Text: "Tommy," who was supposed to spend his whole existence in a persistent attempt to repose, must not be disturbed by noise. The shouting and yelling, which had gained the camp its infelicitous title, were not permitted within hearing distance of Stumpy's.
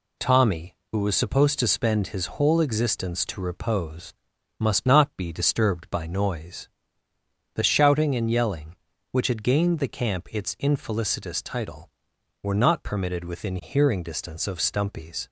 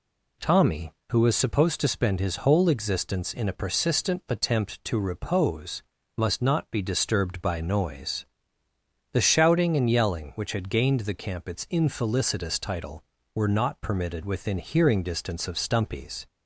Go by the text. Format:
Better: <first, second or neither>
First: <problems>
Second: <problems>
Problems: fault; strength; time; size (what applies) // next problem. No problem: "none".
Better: second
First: skips "in a persistent attempt"; at 3.2 s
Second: none